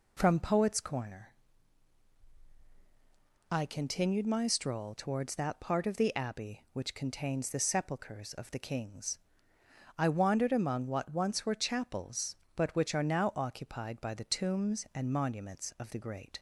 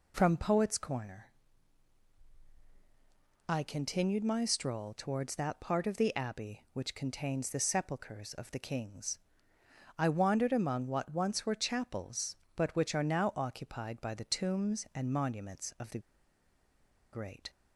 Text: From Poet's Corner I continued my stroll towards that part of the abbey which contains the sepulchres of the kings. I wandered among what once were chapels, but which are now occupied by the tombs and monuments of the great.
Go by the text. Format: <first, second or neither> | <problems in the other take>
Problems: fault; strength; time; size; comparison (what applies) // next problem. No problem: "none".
first | pauses between "Corner" and "I"; strong; at 1.2 s; 2.2 s long; strong in the first // pauses between "the" and "great"; at 15.9 s; 1.1 s long